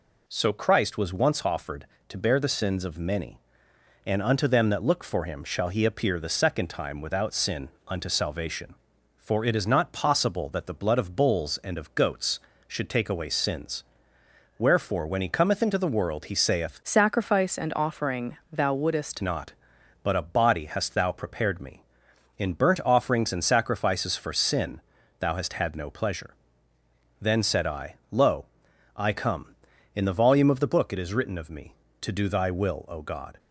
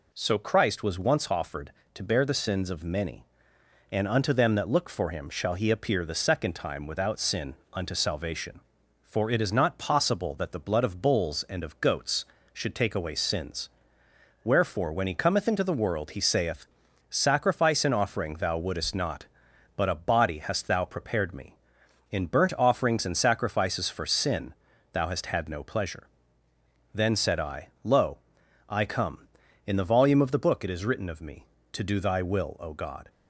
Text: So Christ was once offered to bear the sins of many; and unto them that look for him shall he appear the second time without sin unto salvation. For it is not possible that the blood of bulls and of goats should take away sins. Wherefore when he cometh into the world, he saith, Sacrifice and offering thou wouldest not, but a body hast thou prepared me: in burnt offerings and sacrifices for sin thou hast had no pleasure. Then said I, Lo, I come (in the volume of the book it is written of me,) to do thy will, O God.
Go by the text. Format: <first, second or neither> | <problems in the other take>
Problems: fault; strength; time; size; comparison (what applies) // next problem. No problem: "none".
second | pauses between "sin" and "unto"; slight; at 7.6 s; 0.18 s long; slight in the second // changes voice from "Sacrifice" to "wouldest"; from 16.8 to 19.2 s; 2.4 s long // pauses between "sin" and "thou"; at 24.7 s; 0.40 s long; also in the second